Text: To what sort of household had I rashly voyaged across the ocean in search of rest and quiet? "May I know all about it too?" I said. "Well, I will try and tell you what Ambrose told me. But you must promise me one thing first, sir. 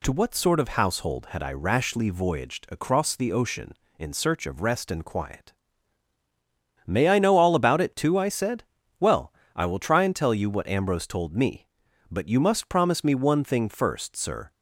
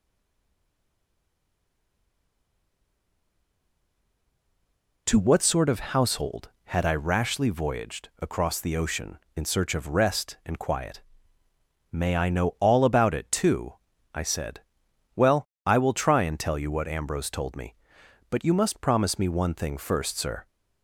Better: first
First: none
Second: stays silent before the first word; strong; until 5.0 s; 5.0 s long

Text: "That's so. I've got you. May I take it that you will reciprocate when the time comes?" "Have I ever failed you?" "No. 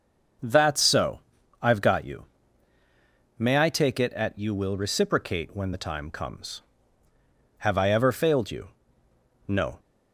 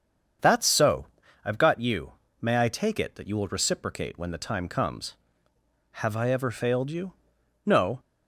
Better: second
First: starts louder than the rest; noticeable; until 1.8 s; 6 dB // says "at" for "that"; at 4.1 s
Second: starts louder than the rest; strong; until 1.7 s; 7 dB

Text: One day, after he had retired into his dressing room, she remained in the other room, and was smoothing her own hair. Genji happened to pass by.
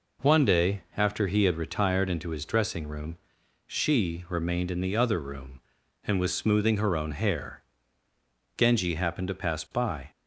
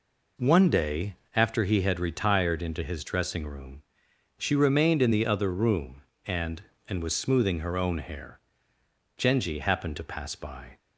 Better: first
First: none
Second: says "and" twice; at 6.8 s

